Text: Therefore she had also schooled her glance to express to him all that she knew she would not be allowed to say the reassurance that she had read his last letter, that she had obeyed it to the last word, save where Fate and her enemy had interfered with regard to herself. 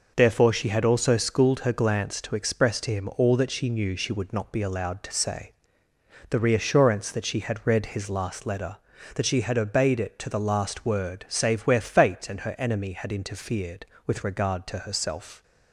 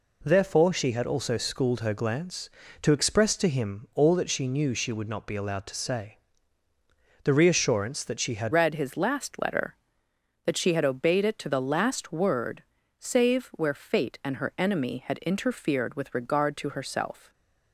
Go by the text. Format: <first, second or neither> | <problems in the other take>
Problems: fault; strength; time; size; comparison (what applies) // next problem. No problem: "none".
first | pauses between "say" and "the"; at 6.1 s; 1.0 s long; noticeable in the first // changes voice at "read"; from 8.5 s on; 8.8 s long